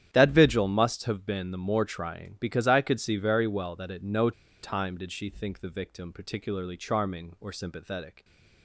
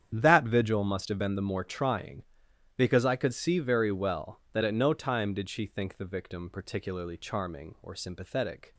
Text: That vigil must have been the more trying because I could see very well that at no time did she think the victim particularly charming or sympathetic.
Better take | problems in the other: second | starts louder than the rest; strong; until 1.1 s; 10.5 dB; strong in the second // pauses between "no" and "time"; slight; at 4.3 s; 0.31 s long

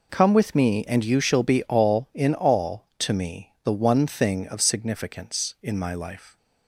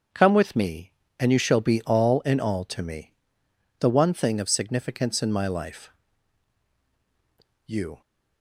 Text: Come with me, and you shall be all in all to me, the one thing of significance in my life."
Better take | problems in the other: first | starts louder than the rest; until 1.3 s; 7 dB // goes on to say "You"; slight; from 7.6 s on; 0.36 s long

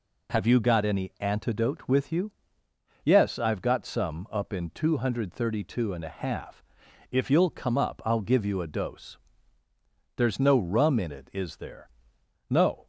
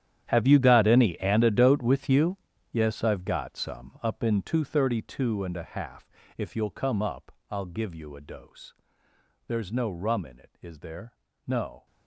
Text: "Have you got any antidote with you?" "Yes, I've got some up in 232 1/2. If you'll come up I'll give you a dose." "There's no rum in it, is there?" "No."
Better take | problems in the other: first | gets quieter; strong; throughout; 18 dB // pauses between "up" and "I'll"; slight; at 7.3 s; 0.18 s long

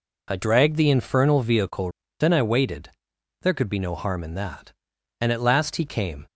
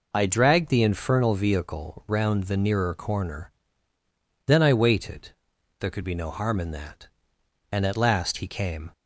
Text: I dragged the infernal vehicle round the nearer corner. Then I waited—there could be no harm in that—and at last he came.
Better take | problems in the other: second | skips "round the nearer corner"; at 2.0 s

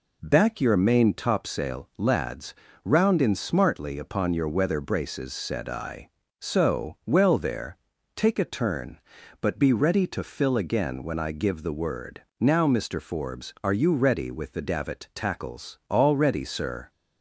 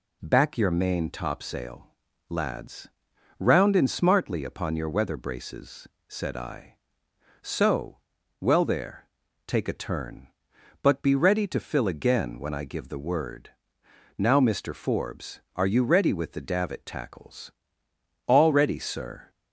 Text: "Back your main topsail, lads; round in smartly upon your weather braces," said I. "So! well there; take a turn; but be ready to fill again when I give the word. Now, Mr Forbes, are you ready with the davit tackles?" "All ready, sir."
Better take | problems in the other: neither | none

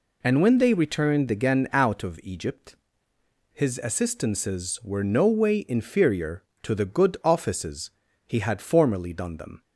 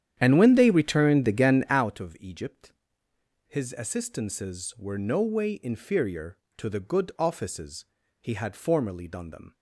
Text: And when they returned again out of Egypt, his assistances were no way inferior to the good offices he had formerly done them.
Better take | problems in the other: first | starts louder than the rest; strong; until 1.9 s; 10 dB // pauses between "offices" and "he"; slight; at 7.8 s; 0.36 s long; slight in the first

